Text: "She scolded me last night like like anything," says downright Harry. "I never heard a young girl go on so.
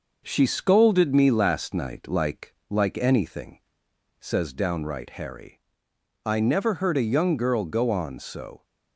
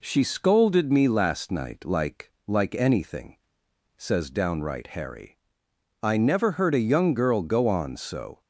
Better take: second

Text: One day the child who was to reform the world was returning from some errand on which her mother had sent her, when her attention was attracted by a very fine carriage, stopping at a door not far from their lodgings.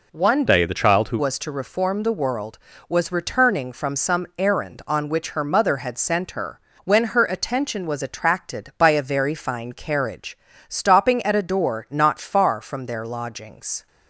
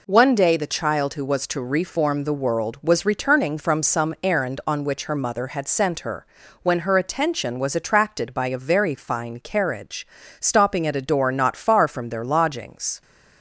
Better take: second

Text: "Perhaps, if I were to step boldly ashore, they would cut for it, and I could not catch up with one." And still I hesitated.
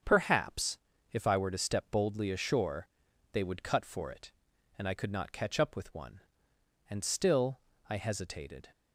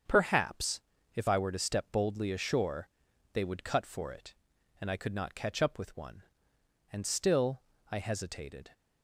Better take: neither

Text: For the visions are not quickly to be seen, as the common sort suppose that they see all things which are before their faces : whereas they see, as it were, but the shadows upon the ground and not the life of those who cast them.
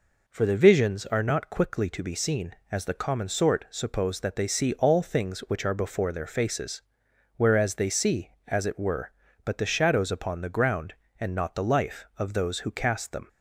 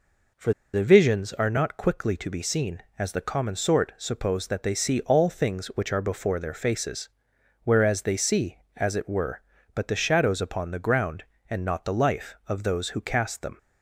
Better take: first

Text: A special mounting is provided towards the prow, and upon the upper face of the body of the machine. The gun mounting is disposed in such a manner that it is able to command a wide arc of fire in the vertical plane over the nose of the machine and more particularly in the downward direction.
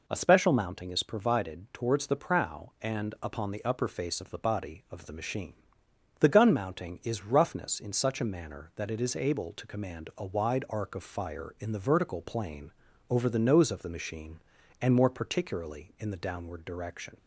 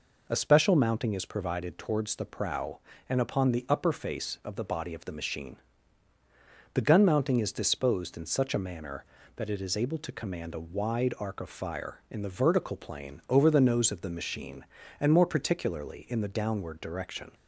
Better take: second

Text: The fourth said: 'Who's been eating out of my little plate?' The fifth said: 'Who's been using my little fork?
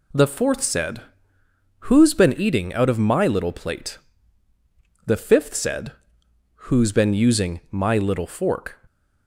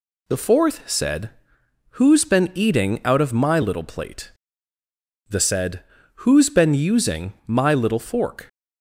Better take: first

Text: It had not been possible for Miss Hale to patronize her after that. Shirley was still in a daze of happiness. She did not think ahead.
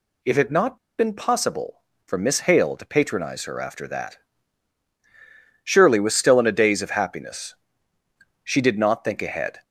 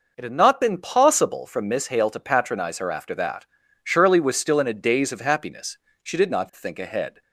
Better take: second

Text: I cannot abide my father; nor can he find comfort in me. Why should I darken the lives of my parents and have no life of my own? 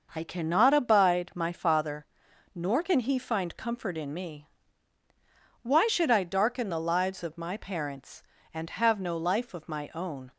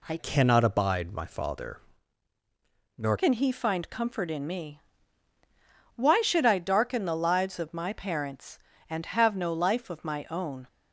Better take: first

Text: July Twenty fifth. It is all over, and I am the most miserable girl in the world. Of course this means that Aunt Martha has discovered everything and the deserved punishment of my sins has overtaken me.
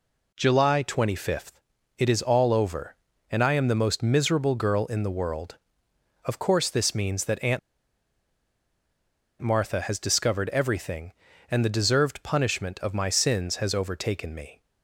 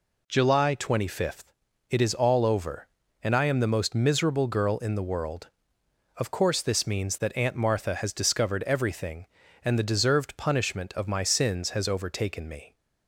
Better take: second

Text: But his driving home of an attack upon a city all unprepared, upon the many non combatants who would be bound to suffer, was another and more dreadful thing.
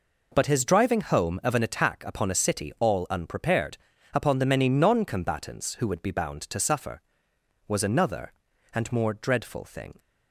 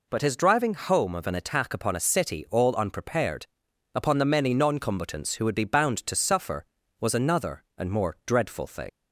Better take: first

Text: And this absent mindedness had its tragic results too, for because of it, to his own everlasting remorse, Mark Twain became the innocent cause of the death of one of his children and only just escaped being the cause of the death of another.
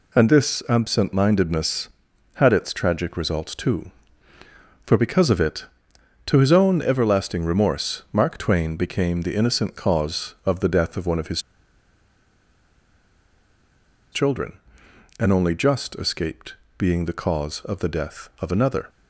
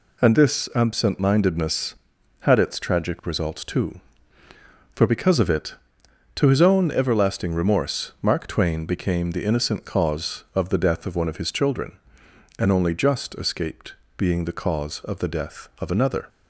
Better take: second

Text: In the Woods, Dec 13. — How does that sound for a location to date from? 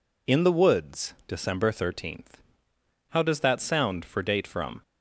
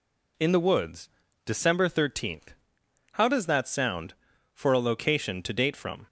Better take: second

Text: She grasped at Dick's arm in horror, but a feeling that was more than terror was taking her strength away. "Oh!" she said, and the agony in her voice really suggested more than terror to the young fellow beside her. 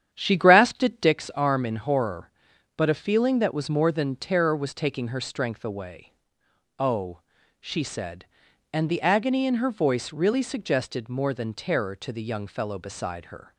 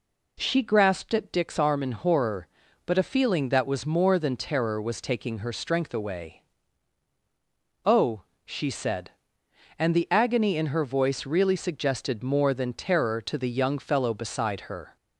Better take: second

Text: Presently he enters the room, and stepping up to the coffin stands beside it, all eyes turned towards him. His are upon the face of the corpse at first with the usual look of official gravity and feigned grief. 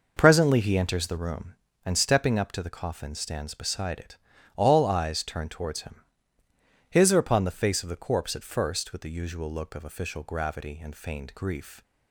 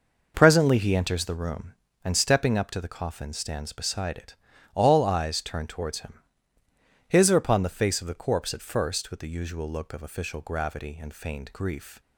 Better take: neither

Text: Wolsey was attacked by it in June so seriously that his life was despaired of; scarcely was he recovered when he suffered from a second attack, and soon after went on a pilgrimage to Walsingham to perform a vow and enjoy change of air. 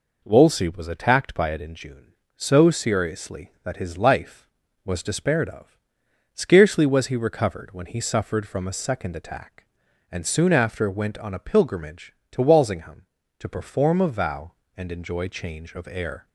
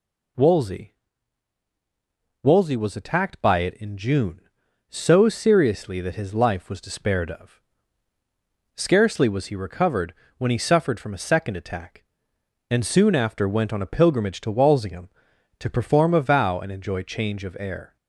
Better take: first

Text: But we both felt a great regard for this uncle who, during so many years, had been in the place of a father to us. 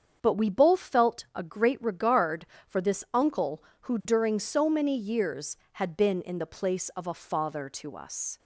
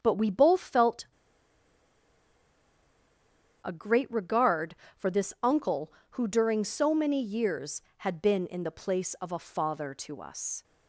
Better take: first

